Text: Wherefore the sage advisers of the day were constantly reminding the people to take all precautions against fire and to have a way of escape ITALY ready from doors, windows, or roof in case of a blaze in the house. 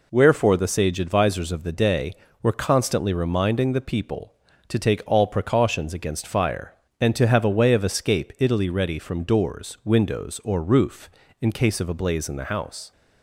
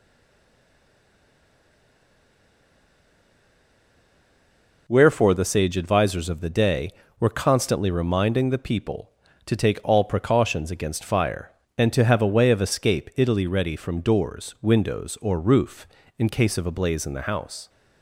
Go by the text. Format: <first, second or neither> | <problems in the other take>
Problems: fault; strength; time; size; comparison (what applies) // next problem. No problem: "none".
first | stays silent before the first word; strong; until 4.8 s; 4.8 s long